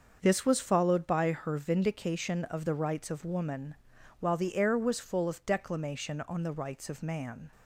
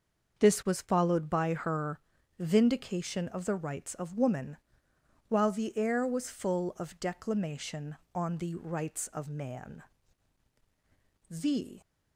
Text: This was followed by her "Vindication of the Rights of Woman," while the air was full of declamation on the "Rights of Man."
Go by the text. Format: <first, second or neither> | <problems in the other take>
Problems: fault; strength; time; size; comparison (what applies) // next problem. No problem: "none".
first | starts louder than the rest; until 1.4 s; 6.5 dB; also in the first // pauses between "her" and "Vindication"; at 1.9 s; 0.40 s long // goes on to say "The"; from 11.2 s on; 0.52 s long